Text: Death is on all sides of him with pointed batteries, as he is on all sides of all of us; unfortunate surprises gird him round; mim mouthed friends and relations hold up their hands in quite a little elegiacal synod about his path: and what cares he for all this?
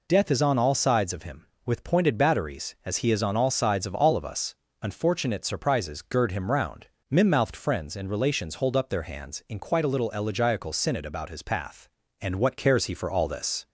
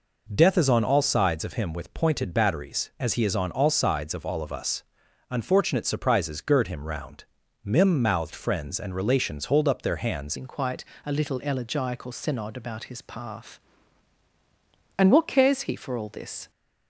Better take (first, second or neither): first